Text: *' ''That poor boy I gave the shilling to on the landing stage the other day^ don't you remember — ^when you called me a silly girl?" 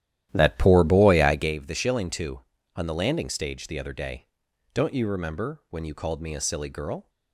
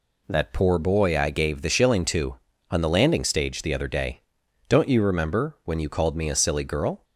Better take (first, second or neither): second